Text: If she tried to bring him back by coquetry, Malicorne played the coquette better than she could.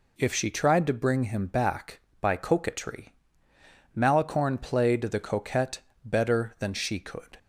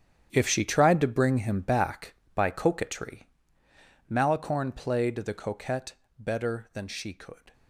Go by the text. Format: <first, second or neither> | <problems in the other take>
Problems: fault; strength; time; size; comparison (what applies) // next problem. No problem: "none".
first | gets quieter; strong; throughout; 14.5 dB // pauses between "coquette" and "better"; slight; at 5.9 s; 0.22 s long; slight in the first